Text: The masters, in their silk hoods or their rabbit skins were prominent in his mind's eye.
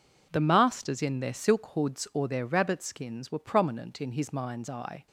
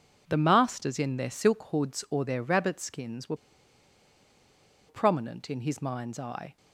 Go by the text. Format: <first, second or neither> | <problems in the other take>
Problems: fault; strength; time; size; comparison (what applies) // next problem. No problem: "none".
first | pauses between "were" and "prominent"; strong; at 3.3 s; 1.5 s long